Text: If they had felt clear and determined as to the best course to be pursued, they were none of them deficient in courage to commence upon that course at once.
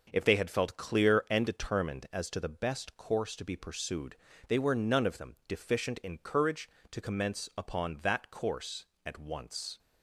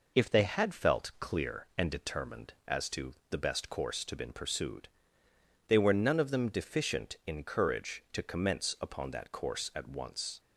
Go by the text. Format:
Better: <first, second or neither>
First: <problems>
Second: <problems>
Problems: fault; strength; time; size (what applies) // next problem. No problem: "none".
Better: first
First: none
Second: pauses between "to" and "the"; slight; at 3.1 s; 0.16 s long // says "been" for "be"; at 4.1 s